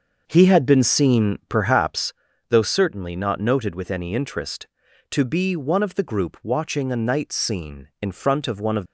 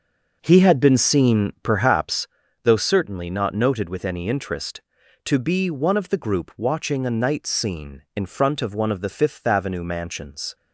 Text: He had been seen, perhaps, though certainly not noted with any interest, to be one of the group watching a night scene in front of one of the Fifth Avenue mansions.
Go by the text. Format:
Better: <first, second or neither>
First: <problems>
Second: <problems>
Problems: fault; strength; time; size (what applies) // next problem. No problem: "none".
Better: second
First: starts louder than the rest; until 1.2 s; 6 dB // stops before "the Fifth Avenue mansions"; at 8.8 s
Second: none